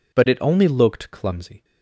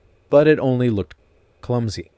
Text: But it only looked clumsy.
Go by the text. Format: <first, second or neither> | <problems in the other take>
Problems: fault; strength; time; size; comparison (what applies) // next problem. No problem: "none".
first | pauses between "looked" and "clumsy"; at 1.1 s; 0.45 s long